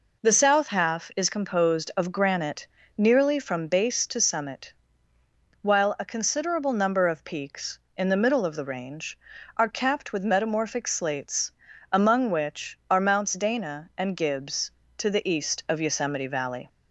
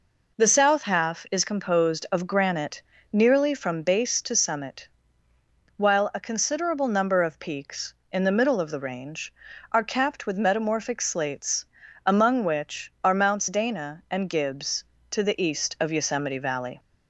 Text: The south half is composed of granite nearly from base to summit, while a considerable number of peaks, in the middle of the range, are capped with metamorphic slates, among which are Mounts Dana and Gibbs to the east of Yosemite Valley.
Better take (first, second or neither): neither